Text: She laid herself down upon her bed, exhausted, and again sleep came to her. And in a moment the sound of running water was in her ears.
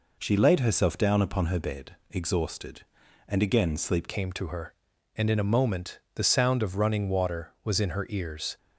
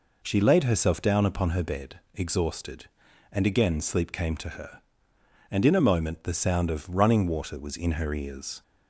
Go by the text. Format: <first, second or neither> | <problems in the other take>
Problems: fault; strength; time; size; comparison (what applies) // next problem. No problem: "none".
second | changes voice at "came"; from 4.0 s on; 4.5 s long // pauses between "moment" and "the"; slight; at 5.9 s; 0.16 s long